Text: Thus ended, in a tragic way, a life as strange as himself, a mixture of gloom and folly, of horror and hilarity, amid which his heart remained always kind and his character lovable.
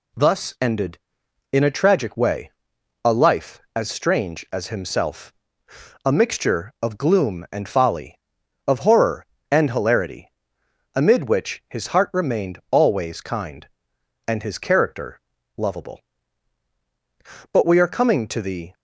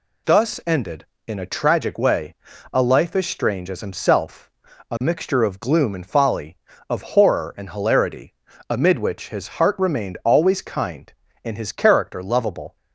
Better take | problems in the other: second | pauses between "character" and "lovable"; slight; at 15.1 s; 0.36 s long // goes on to say "But we are coming to the"; noticeable; from 17.5 s on; 1.2 s long

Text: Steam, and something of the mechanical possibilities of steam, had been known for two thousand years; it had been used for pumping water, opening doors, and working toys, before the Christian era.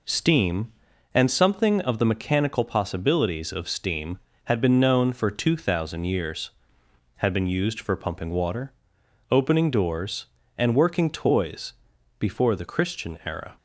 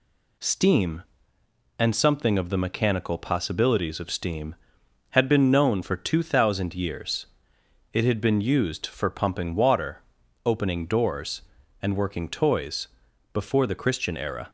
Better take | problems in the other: second | skips "it"; at 6.8 s

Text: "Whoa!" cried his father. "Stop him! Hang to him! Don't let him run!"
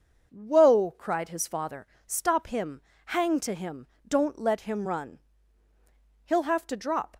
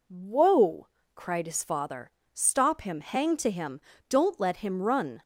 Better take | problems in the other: second | goes on to say "He'll have to drop"; noticeable; from 6.2 s on; 0.94 s long

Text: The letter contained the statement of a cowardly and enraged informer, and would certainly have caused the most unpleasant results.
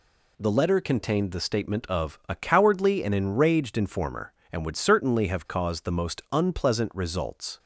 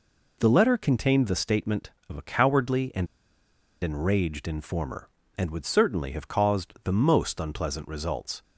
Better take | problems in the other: first | pauses between "and" and "enraged"; noticeable; at 3.0 s; 0.76 s long

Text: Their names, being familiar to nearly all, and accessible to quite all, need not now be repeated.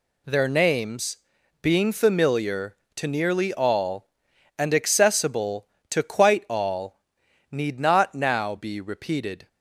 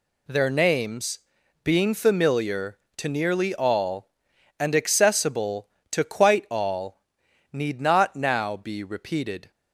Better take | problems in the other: neither | none

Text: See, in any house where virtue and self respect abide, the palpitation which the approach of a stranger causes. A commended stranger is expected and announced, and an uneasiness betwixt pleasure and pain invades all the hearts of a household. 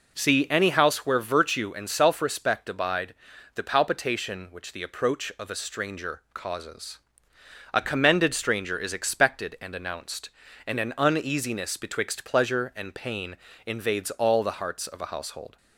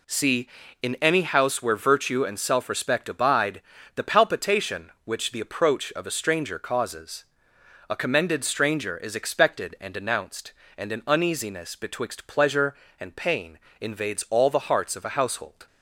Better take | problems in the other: second | skips "in"; at 0.4 s // pauses between "pain" and "invades"; slight; at 13.3 s; 0.32 s long; slight in the second

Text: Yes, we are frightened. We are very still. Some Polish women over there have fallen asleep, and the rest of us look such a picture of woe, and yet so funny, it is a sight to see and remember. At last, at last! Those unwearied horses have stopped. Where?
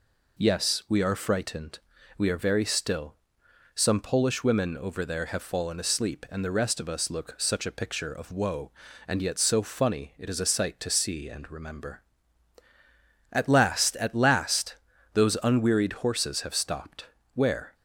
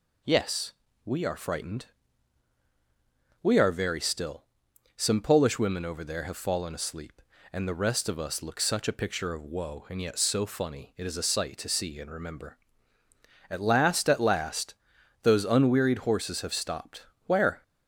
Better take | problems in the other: neither | none

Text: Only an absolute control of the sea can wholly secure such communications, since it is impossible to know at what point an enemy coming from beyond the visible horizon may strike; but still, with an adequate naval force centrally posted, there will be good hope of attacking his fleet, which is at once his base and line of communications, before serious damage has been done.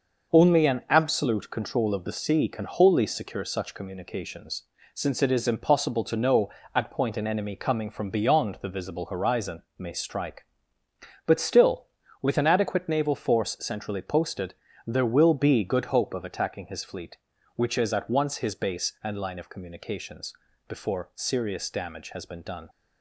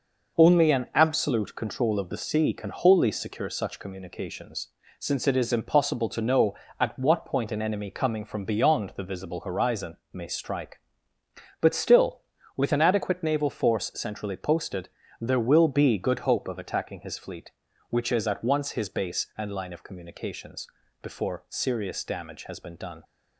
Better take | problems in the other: second | skips "what"; at 6.9 s // pauses between "horizon" and "may"; slight; at 9.6 s; 0.16 s long; slight in the second

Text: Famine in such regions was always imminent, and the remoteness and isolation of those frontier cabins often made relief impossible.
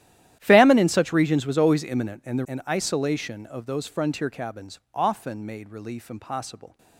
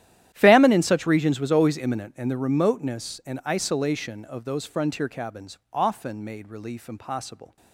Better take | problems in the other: second | starts louder than the rest; strong; until 1.4 s; 12.5 dB; strong in the second // skips "remoteness"; at 2.4 s

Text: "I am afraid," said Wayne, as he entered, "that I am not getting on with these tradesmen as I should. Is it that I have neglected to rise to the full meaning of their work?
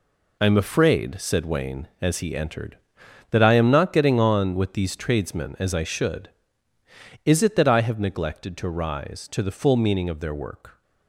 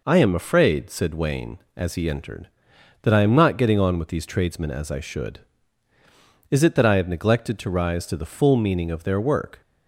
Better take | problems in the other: second | gets quieter; strong; throughout; 9 dB

